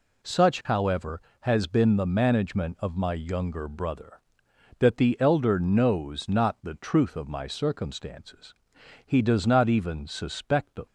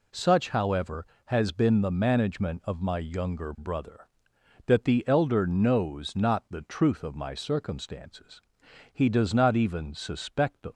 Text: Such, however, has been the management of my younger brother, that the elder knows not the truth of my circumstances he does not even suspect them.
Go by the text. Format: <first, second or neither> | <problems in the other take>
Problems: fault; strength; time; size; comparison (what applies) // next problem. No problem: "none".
neither | pauses between "circumstances" and "he"; noticeable; the same in both